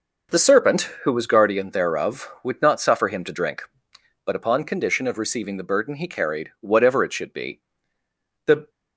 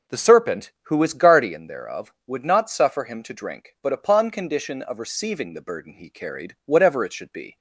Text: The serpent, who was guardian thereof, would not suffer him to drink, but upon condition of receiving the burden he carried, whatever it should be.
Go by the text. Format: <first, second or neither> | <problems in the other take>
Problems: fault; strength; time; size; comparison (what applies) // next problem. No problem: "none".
second | goes on to say "The"; slight; from 8.4 s on; 0.24 s long